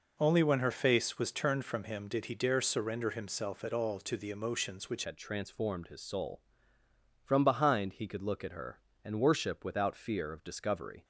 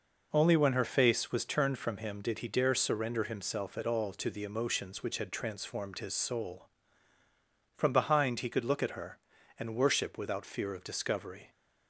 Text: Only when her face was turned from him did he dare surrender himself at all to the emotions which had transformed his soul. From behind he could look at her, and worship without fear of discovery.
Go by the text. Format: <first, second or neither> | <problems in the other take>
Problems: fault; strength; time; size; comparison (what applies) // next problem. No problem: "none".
second | changes voice at "had"; from 5.0 s on; 6.0 s long